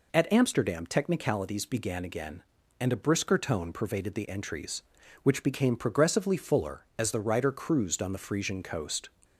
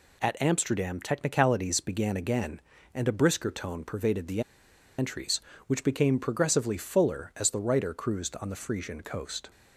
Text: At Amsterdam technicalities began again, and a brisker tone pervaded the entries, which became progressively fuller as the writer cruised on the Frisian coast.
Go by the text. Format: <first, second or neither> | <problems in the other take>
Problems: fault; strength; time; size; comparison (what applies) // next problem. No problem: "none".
first | pauses between "the" and "entries"; noticeable; at 4.4 s; 0.57 s long